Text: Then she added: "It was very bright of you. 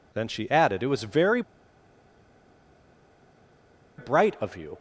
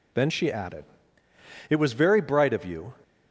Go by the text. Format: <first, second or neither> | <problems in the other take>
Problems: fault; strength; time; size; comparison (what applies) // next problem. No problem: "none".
second | pauses between "very" and "bright"; strong; at 1.4 s; 2.5 s long